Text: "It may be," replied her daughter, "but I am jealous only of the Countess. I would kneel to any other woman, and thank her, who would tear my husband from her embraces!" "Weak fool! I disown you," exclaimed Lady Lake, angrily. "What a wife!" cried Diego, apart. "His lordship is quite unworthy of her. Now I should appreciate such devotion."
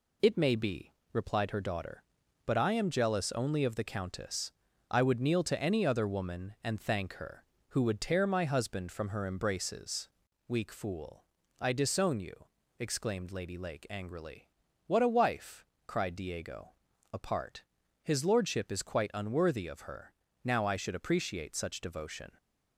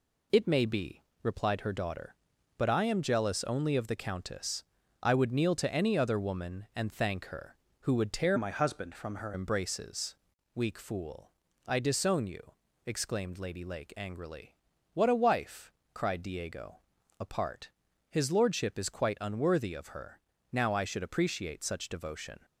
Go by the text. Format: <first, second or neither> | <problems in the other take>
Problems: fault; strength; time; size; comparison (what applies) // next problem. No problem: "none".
first | changes voice from "my" to "her"; from 8.3 to 9.3 s; 1.0 s long